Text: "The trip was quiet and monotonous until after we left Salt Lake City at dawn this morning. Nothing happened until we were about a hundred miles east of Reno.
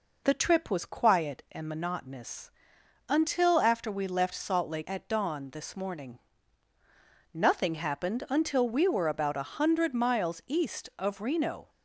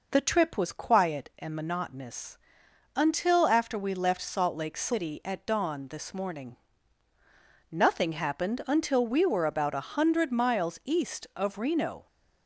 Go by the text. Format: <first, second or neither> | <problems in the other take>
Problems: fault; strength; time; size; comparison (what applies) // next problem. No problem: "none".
second | pauses between "monotonous" and "until"; noticeable; at 2.5 s; 0.56 s long; noticeable in the second // skips "City"; at 4.8 s